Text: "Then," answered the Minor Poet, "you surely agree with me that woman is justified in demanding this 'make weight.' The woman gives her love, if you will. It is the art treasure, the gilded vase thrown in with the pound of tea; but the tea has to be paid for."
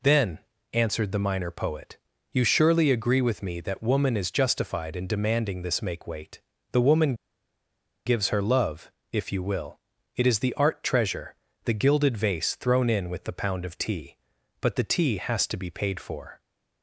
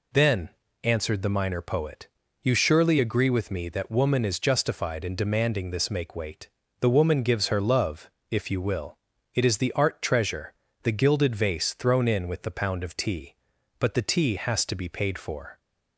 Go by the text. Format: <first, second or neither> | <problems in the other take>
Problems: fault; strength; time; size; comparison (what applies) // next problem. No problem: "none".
second | pauses between "woman" and "gives"; noticeable; at 7.1 s; 0.91 s long